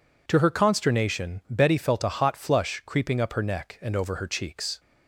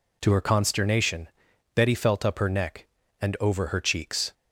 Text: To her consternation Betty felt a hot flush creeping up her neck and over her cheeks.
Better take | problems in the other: first | pauses between "consternation" and "Betty"; noticeable; at 1.2 s; 0.46 s long // skips "a hot flush creeping"; at 2.2 s

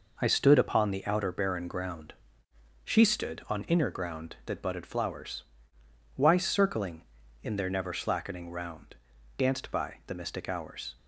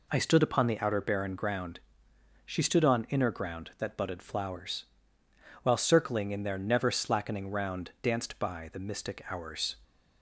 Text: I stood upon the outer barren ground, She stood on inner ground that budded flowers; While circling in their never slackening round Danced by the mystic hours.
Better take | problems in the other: second | says "Why" for "While"; at 6.1 s // pauses between "round" and "Danced"; at 8.9 s; 0.40 s long

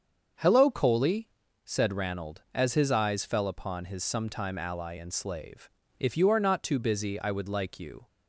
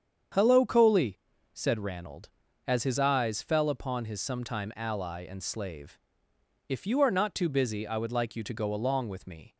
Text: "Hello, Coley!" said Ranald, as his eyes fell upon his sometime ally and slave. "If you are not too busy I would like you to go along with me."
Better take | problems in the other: second | starts louder than the rest; until 1.7 s; 7 dB; strong in the second // stops before "to go along with me"; at 8.0 s

